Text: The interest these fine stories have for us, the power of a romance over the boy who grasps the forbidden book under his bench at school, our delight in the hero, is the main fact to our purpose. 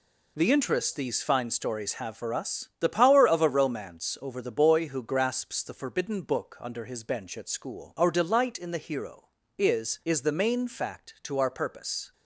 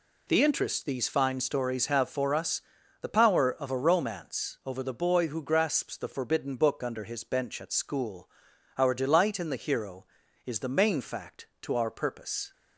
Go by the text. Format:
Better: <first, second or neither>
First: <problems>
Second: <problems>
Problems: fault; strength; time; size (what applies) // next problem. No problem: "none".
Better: second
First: says "is" twice; at 10.0 s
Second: none